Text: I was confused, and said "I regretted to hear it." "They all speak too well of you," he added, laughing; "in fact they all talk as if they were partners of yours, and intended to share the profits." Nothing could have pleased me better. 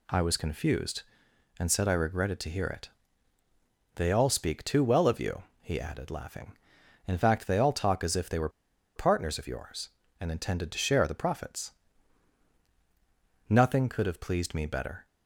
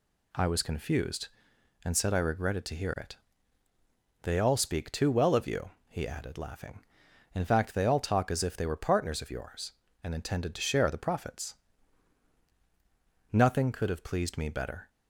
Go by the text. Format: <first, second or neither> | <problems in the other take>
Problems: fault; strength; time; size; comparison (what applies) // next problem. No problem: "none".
second | pauses between "were" and "partners"; noticeable; at 8.4 s; 0.46 s long